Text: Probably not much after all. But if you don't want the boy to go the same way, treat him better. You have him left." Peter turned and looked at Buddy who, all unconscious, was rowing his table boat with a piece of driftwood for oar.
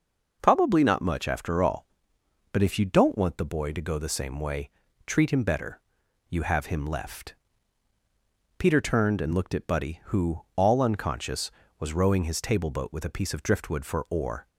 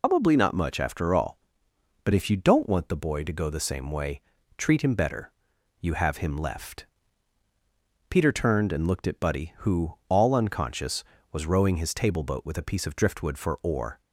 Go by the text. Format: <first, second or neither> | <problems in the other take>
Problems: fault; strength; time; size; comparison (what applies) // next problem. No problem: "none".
first | loses the start of "Probably"; at 0.0 s; 110 ms